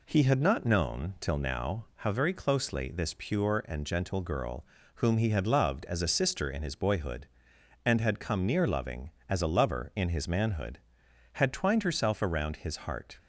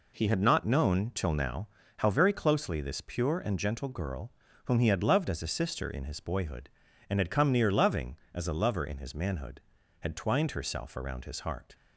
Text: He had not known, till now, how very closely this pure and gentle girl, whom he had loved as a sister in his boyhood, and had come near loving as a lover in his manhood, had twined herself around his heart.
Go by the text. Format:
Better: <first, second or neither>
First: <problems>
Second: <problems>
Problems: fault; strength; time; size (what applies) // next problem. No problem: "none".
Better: neither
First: none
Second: none